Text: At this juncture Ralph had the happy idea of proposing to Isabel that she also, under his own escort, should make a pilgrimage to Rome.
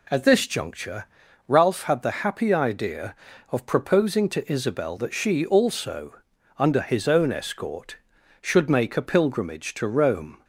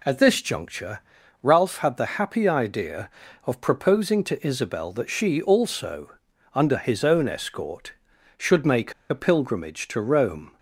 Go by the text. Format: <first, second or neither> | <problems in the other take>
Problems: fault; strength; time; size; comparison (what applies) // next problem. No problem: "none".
first | pauses between "juncture" and "Ralph"; at 0.9 s; 0.44 s long; also in the first // pauses between "make" and "a"; slight; at 8.9 s; 0.17 s long